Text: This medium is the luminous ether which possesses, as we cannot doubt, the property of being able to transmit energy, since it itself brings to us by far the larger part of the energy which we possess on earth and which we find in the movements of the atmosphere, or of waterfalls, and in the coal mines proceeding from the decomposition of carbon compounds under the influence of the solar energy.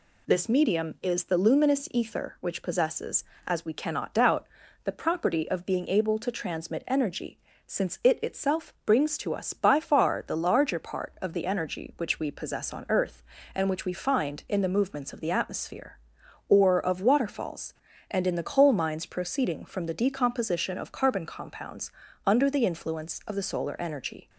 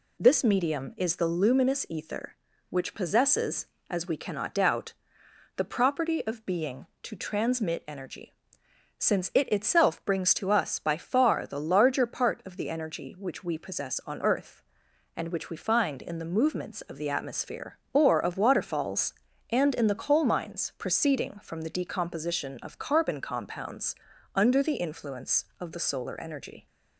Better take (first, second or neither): first